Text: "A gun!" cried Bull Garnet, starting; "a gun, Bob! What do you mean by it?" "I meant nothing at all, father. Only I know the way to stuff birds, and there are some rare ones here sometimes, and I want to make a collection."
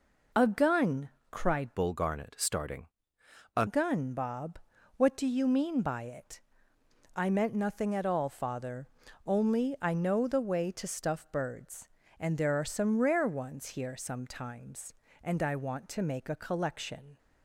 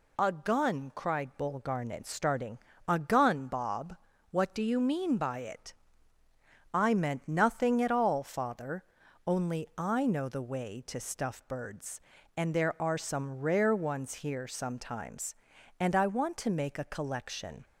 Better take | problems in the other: second | changes voice from "Bull" to "a"; from 1.7 to 3.6 s; 1.9 s long

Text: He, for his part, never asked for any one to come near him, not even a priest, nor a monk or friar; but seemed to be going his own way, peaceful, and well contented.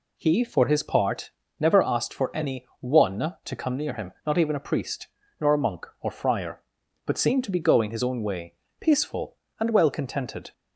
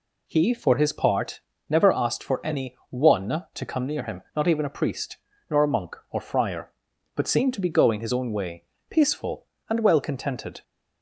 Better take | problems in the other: neither | none

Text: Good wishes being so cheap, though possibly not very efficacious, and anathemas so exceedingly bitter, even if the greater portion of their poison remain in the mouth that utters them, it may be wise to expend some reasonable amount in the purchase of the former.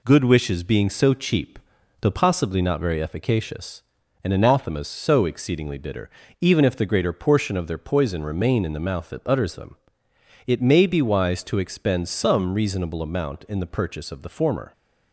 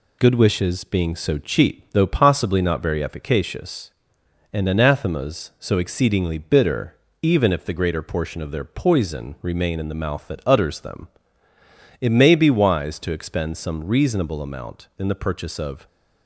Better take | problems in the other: first | stops before "the former"; at 15.8 s

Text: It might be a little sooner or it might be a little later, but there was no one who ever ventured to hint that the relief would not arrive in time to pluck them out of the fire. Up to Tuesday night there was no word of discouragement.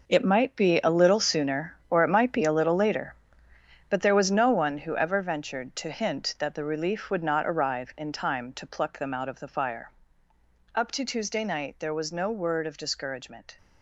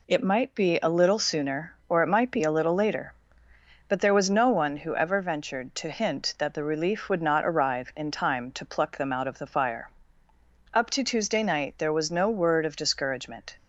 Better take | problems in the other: second | gets quieter; strong; throughout; 12 dB

